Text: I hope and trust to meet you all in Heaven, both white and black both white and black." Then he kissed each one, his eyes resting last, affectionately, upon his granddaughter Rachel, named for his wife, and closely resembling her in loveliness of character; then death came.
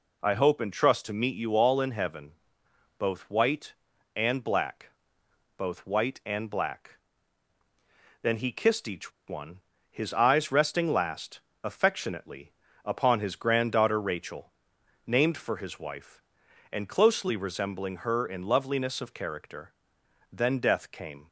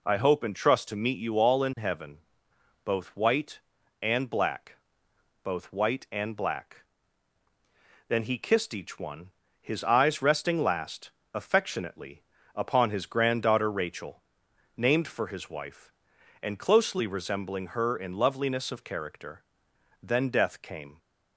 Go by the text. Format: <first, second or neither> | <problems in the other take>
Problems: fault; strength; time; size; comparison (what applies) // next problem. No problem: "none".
second | pauses between "black" and "both"; noticeable; at 4.8 s; 0.68 s long; noticeable in the second // pauses between "each" and "one"; slight; at 9.1 s; 0.15 s long